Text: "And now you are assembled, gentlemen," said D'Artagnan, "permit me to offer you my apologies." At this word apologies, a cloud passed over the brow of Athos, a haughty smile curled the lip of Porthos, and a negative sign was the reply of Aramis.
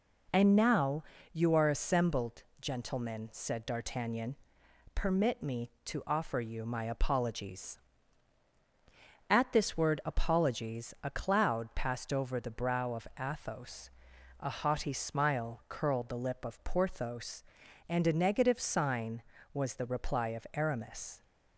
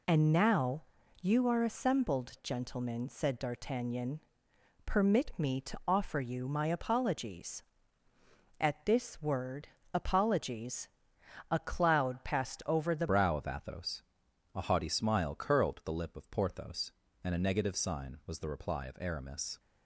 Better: first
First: pauses between "now" and "you"; slight; at 1.0 s; 0.28 s long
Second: pauses between "now" and "you"; at 0.8 s; 0.38 s long // pauses between "word" and "apologies"; slight; at 9.6 s; 0.26 s long // changes voice at "brow"; from 13.0 s on; 6.5 s long

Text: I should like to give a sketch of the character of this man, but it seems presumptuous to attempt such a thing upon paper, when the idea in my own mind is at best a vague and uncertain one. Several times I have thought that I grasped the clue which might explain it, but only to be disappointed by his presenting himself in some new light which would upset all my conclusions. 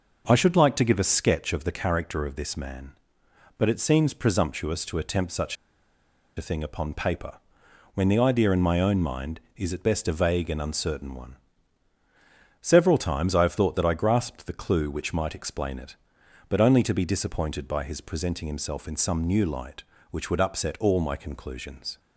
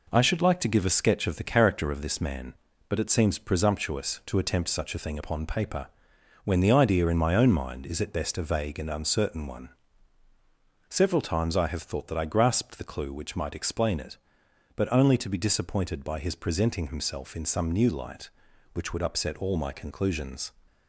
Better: second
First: pauses between "such" and "a"; noticeable; at 5.5 s; 0.81 s long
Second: none

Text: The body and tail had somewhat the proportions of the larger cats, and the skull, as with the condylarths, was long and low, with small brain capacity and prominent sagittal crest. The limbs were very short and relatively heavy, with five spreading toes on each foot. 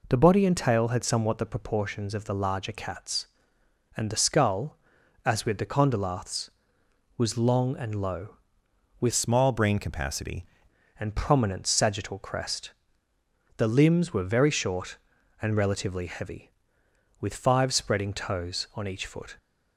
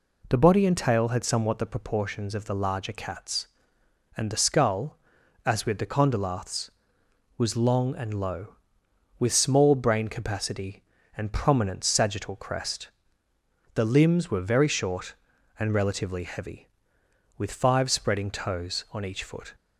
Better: second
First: changes voice from "small" to "capacity"; from 9.1 to 10.4 s; 1.3 s long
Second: none

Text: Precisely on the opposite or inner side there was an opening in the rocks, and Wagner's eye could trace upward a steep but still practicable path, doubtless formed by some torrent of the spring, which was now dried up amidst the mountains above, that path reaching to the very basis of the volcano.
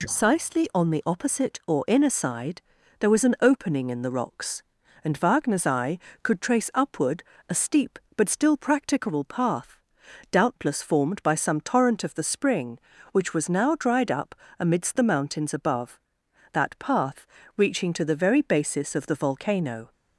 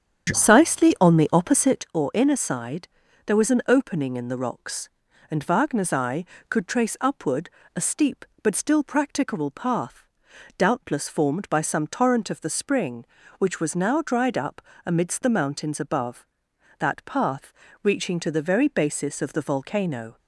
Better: first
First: pauses between "side" and "there"; at 2.5 s; 0.38 s long // pauses between "upward" and "a"; slight; at 7.2 s; 0.26 s long // pauses between "up" and "amidst"; slight; at 14.3 s; 0.24 s long // pauses between "path" and "reaching"; slight; at 17.2 s; 0.32 s long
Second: starts louder than the rest; strong; until 2.0 s; 8.5 dB // pauses between "side" and "there"; at 2.8 s; 0.38 s long // pauses between "upward" and "a"; slight; at 7.4 s; 0.26 s long // pauses between "up" and "amidst"; slight; at 14.6 s; 0.24 s long // pauses between "path" and "reaching"; slight; at 17.5 s; 0.32 s long

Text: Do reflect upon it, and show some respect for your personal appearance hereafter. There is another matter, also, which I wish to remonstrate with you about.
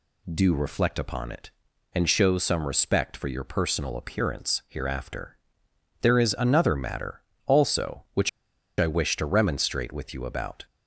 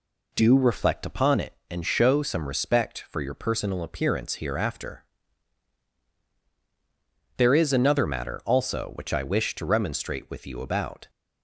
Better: second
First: pauses between "which" and "I"; noticeable; at 8.2 s; 0.49 s long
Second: none

